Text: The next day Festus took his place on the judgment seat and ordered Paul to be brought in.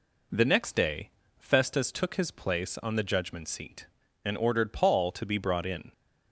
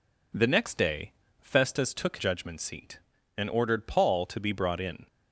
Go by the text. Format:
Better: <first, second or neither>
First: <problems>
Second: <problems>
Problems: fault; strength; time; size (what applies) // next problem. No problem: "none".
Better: first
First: pauses between "day" and "Festus"; slight; at 1.1 s; 0.28 s long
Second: pauses between "day" and "Festus"; slight; at 1.1 s; 0.28 s long // skips "his place on the"; at 2.1 s